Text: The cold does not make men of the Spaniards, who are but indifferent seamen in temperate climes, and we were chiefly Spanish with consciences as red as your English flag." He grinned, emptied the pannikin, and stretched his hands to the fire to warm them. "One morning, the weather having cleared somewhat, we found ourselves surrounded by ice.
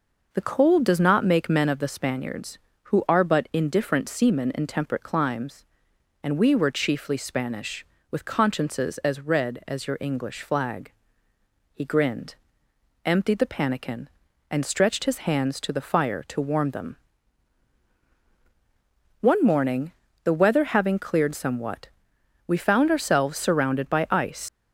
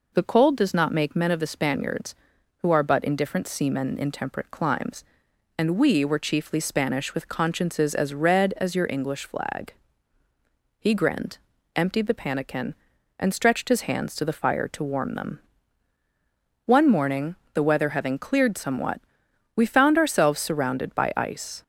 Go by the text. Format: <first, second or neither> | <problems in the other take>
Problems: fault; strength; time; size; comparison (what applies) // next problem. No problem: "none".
second | leaves "ice" unfinished; at 24.4 s; 125 ms